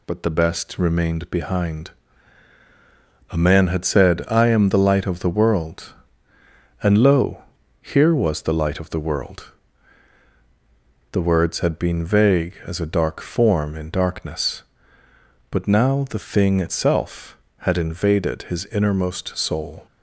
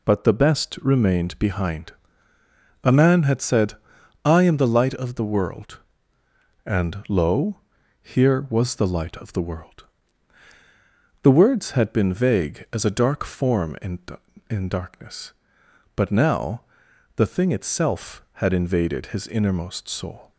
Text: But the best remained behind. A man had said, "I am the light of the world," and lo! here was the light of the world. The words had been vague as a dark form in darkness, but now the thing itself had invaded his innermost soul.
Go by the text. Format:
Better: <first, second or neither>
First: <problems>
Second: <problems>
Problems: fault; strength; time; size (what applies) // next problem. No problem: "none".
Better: first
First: none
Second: says "in" twice; at 14.5 s // pauses between "now" and "the"; noticeable; at 16.6 s; 0.56 s long